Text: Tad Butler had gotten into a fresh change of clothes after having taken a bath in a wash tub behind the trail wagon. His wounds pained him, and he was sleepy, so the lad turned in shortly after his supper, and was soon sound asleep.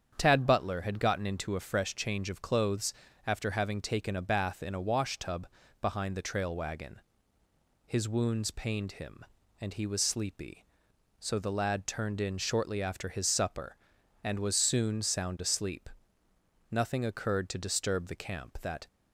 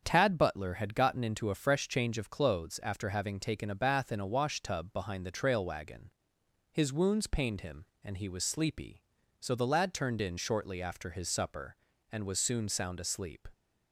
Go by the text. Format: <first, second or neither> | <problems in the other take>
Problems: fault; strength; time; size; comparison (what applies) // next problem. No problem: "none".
second | starts louder than the rest; strong; until 1.1 s; 7.5 dB; strong in the second // pauses between "clothes" and "after"; slight; at 2.9 s; 0.32 s long // pauses between "tub" and "behind"; slight; at 5.4 s; 0.34 s long // goes on to say "Nothing occurred to disturb the camp that"; strong; from 16.7 s on; 2.1 s long